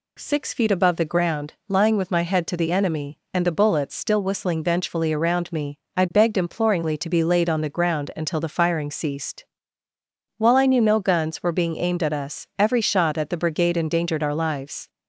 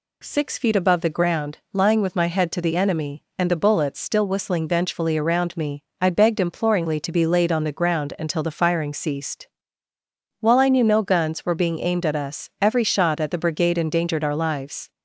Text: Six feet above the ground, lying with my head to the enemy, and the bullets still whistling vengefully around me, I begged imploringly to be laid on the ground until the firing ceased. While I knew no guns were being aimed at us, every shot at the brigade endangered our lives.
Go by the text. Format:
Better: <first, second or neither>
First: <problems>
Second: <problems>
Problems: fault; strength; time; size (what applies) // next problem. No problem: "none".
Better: neither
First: none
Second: none